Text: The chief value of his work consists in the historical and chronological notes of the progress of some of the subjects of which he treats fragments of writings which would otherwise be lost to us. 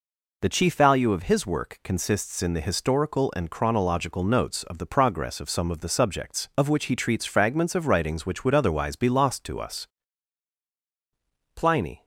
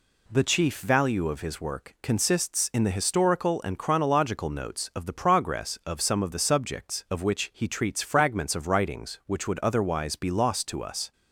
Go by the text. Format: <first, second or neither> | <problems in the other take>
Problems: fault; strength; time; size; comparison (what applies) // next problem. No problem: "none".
second | goes on to say "Pliny"; slight; from 11.5 s on; 0.48 s long